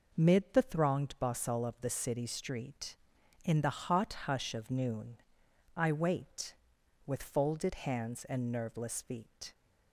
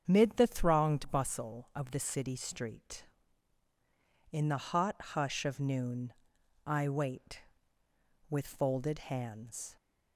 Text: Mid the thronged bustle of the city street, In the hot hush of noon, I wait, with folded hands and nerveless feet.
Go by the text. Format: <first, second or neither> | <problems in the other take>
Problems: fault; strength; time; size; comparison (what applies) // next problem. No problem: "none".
first | starts louder than the rest; strong; until 1.0 s; 7.5 dB // stops before "and nerveless feet"; at 9.7 s